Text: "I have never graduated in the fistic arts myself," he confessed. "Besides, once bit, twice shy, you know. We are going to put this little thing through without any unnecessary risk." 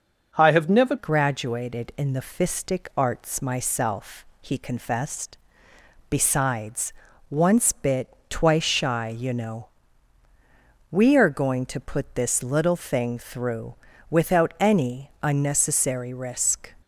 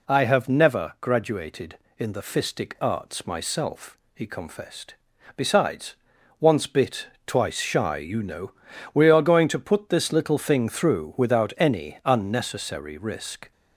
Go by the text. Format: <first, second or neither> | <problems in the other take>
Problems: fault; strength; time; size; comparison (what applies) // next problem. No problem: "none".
second | changes voice at "graduated"; from 0.9 s on; 15.8 s long // pauses between "through" and "without"; slight; at 13.7 s; 0.34 s long